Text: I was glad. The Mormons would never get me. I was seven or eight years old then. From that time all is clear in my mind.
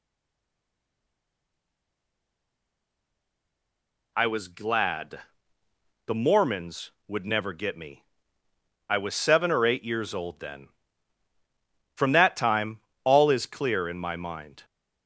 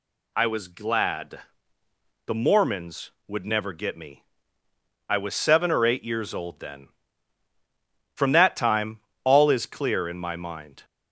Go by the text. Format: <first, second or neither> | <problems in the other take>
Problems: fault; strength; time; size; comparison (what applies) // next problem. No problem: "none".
second | stays silent before the first word; strong; until 4.1 s; 4.1 s long // pauses between "time" and "all"; slight; at 12.8 s; 0.24 s long; slight in the second